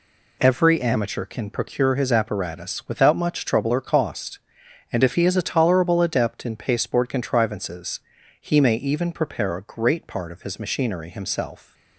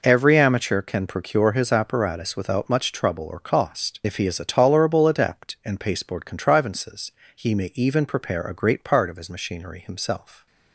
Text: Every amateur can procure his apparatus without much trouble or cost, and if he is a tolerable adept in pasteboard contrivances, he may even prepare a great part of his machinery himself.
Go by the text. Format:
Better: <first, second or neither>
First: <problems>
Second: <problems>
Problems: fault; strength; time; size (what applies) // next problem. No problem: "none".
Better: first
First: none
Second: skips "and"; at 4.0 s